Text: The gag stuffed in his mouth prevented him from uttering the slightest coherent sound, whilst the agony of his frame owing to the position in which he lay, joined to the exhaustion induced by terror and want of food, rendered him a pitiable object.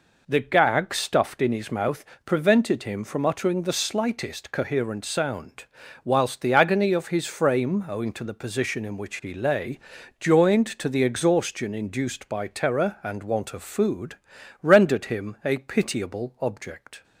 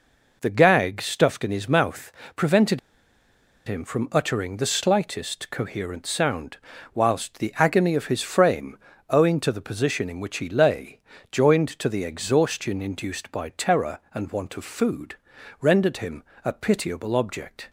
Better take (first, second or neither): first